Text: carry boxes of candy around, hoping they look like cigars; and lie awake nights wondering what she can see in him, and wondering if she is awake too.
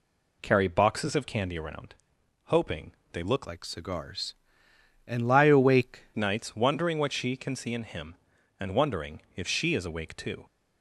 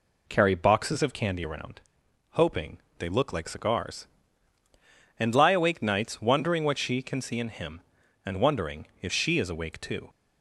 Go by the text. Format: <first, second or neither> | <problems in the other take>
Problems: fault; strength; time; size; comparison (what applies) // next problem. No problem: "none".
second | pauses between "hoping" and "they"; slight; at 2.9 s; 0.20 s long; slight in the second // changes voice from "like" to "awake"; from 3.4 to 6.0 s; 2.6 s long